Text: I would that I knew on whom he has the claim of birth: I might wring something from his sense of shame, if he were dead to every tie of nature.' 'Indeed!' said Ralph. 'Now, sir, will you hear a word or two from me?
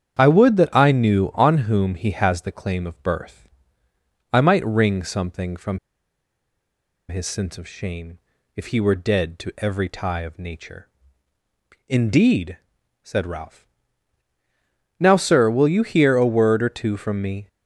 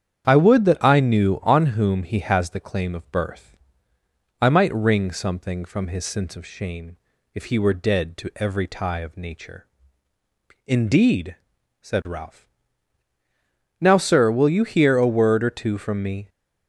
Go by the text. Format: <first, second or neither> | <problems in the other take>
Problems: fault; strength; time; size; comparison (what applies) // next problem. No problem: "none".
second | starts louder than the rest; strong; until 1.2 s; 8.5 dB; strong in the second // pauses between "from" and "his"; strong; at 5.7 s; 1.3 s long